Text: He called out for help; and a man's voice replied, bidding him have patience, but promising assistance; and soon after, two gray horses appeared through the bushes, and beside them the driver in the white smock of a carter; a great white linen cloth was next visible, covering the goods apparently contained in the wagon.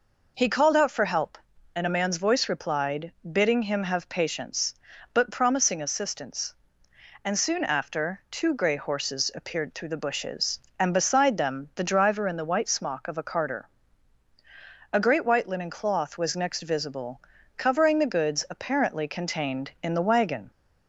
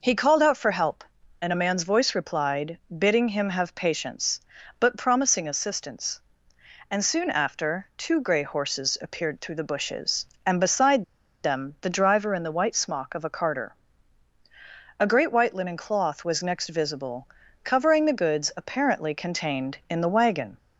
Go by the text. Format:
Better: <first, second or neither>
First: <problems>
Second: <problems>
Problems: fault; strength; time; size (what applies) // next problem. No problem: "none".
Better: first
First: none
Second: pauses between "beside" and "them"; at 11.0 s; 0.40 s long